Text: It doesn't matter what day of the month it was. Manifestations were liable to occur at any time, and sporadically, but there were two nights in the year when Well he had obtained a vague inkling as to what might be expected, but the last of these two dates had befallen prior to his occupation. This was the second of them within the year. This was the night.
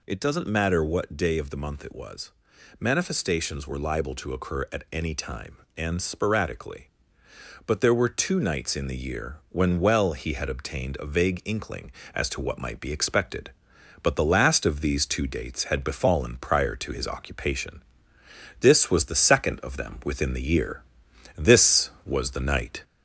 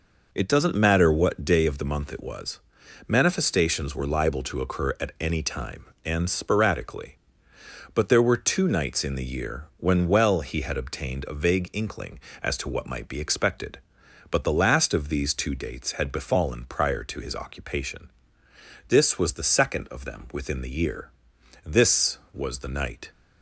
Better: second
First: gets louder; slight; throughout; 2 dB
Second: none

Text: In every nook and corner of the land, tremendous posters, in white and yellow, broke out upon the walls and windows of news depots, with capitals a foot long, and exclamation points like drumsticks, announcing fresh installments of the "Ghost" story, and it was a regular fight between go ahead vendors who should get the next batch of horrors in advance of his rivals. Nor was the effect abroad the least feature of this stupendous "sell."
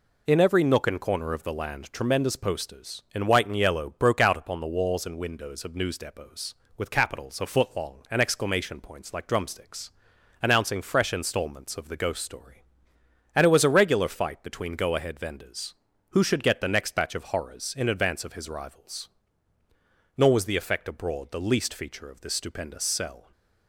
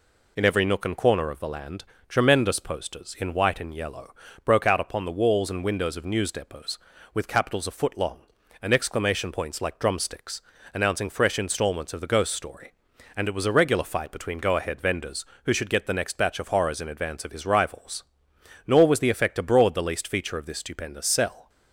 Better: neither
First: none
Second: none

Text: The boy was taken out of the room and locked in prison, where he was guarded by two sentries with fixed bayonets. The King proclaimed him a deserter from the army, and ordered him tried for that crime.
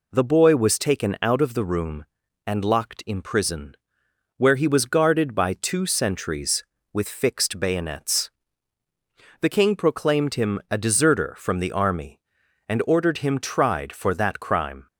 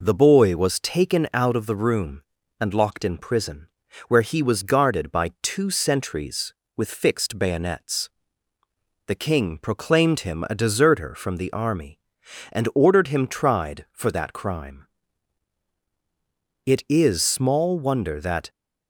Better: first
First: none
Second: goes on to say "It is small wonder that"; strong; from 16.6 s on; 1.8 s long

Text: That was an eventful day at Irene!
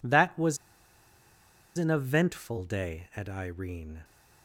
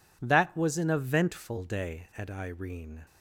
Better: second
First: pauses between "was" and "an"; at 0.5 s; 1.2 s long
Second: none

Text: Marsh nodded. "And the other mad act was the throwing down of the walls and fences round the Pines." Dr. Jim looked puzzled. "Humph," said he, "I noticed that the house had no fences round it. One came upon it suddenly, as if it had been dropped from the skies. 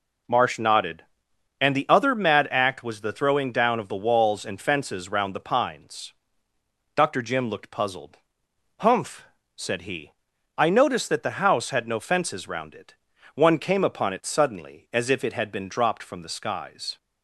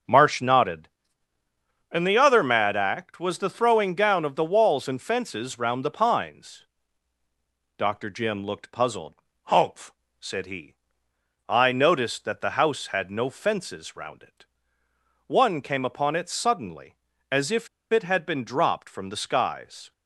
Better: first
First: none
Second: starts louder than the rest; until 2.0 s; 6 dB // pauses between "if" and "it"; slight; at 17.6 s; 0.24 s long

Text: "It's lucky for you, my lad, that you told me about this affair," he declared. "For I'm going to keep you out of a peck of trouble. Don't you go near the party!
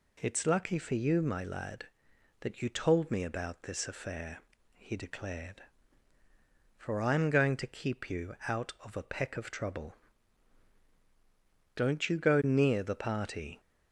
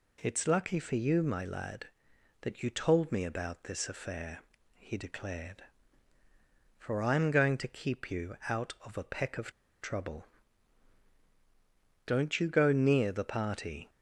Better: first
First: none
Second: pauses between "of" and "trouble"; slight; at 9.5 s; 0.30 s long

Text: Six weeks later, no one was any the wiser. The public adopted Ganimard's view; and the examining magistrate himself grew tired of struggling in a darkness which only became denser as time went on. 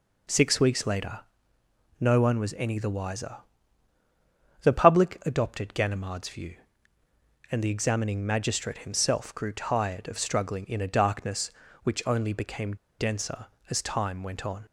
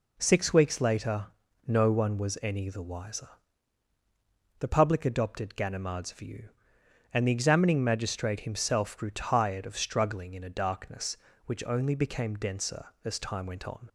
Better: second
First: pauses between "became" and "denser"; slight; at 12.7 s; 0.23 s long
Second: none

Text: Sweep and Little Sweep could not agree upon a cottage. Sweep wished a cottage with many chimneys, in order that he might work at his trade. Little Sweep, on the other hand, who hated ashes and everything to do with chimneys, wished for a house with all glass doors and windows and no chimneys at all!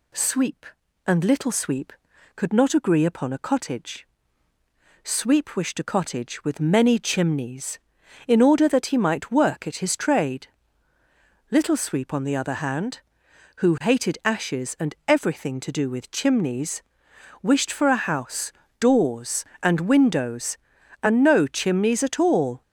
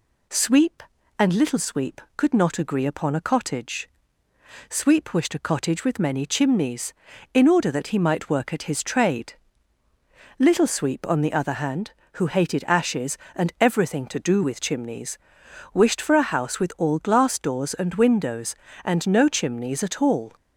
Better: second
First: skips "with all glass"; at 18.6 s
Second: none

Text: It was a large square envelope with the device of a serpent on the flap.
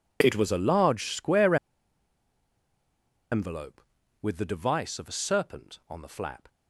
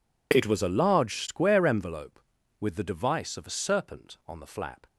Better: second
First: pauses between "square" and "envelope"; strong; at 1.5 s; 1.7 s long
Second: none

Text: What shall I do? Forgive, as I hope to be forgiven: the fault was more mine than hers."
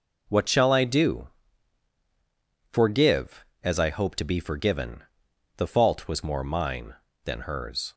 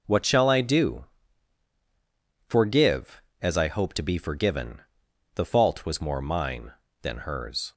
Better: neither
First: none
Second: none

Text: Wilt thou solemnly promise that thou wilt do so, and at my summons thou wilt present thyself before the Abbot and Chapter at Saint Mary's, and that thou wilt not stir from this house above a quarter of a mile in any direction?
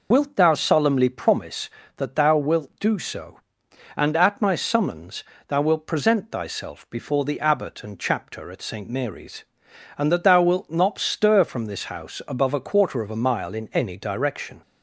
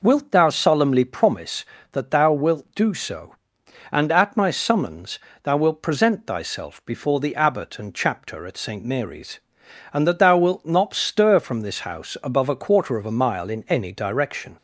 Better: second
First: loses the start of "Wilt"; at 0.1 s; 30 ms // pauses between "summons" and "thou"; slight; at 5.2 s; 0.24 s long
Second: pauses between "summons" and "thou"; slight; at 5.2 s; 0.24 s long

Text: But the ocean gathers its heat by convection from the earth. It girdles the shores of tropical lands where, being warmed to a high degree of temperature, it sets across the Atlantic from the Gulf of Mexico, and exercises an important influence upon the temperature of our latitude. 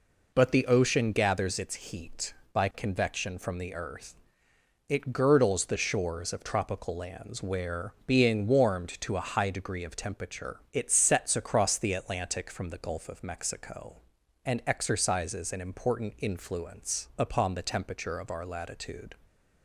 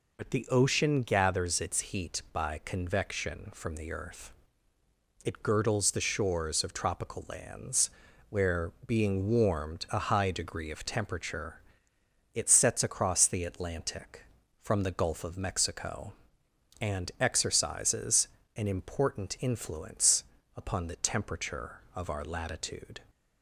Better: first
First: none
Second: pauses between "lands" and "where"; at 7.8 s; 0.40 s long // skips "to"; at 9.8 s // pauses between "exercises" and "an"; slight; at 18.2 s; 0.28 s long // pauses between "influence" and "upon"; slight; at 20.2 s; 0.34 s long

